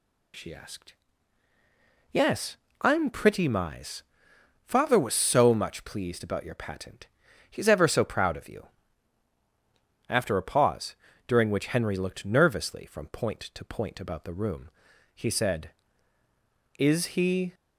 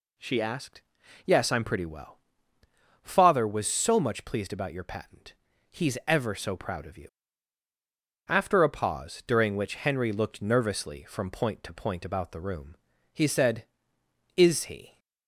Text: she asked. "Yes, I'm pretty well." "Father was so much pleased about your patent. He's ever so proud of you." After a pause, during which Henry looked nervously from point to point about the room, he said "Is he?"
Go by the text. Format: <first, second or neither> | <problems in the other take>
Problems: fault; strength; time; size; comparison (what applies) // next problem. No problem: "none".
second | says "mize" for "well"; at 3.4 s